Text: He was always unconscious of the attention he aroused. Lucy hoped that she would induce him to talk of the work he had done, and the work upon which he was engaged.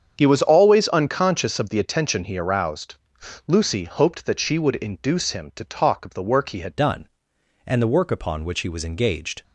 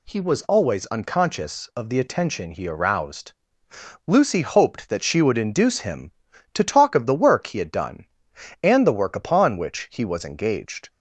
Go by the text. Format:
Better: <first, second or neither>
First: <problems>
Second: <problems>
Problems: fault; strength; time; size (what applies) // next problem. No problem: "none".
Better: second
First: starts louder than the rest; strong; until 1.1 s; 7.5 dB // changes voice at "done"; from 6.7 s on; 2.7 s long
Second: none